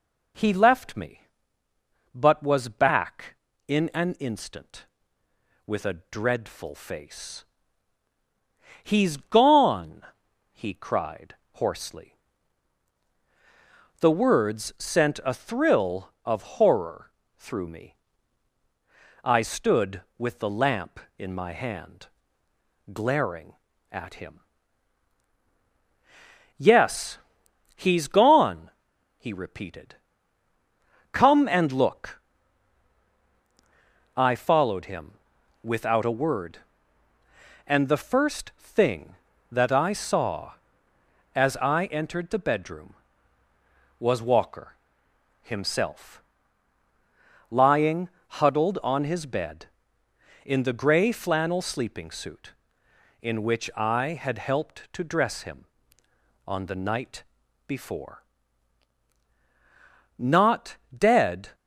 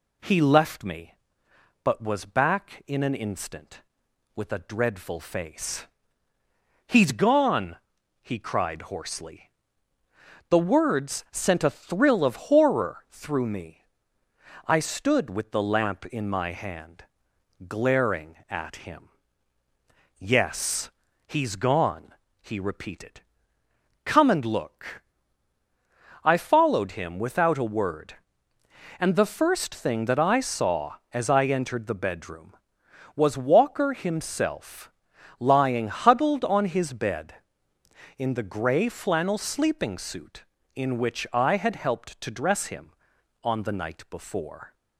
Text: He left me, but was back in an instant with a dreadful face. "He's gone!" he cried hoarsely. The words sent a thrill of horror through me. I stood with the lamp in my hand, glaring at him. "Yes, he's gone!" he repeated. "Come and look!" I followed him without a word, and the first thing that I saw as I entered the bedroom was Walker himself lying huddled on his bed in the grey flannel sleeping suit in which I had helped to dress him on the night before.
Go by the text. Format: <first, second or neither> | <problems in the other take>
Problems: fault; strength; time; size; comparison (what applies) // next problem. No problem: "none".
second | pauses between "cried" and "hoarsely"; slight; at 11.3 s; 0.18 s long // pauses between "horror" and "through"; slight; at 17.1 s; 0.26 s long // pauses between "him" and "without"; noticeable; at 35.1 s; 0.50 s long // pauses between "Walker" and "himself"; noticeable; at 44.7 s; 0.68 s long // pauses between "himself" and "lying"; strong; at 46.2 s; 1.2 s long; noticeable in the second // pauses between "lying" and "huddled"; slight; at 48.0 s; 0.34 s long // pauses between "night" and "before"; noticeable; at 57.2 s; 0.46 s long // goes on to say "Not dead"; from 60.1 s on; 1.3 s long